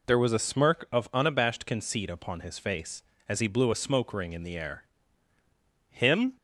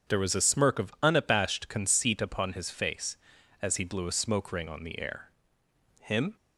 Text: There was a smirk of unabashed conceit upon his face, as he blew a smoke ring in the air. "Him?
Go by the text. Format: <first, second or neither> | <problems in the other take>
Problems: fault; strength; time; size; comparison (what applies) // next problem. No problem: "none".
first | starts louder than the rest; strong; until 1.1 s; 7.5 dB // says "on" for "in"; at 4.6 s